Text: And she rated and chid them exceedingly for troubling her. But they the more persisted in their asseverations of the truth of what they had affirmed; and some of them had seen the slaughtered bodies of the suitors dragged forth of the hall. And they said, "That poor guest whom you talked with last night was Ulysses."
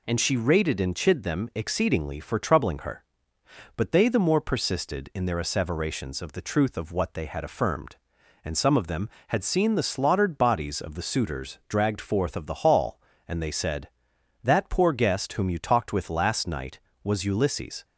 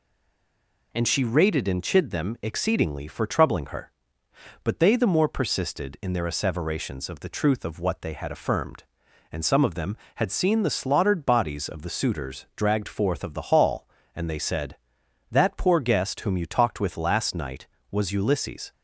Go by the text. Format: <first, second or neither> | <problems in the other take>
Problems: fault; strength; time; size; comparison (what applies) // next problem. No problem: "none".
first | stays silent before the first word; slight; until 0.9 s; 0.9 s long